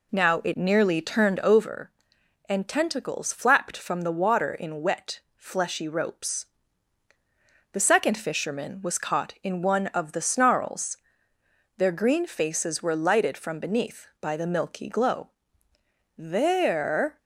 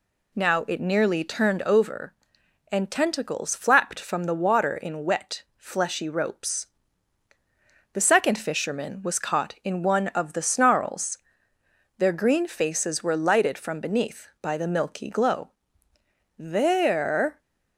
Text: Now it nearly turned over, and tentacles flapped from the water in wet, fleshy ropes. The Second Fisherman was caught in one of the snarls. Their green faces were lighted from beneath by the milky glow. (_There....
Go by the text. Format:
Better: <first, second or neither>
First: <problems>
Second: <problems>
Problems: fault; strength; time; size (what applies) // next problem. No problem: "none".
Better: second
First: starts louder than the rest; slight; until 1.8 s; 3 dB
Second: none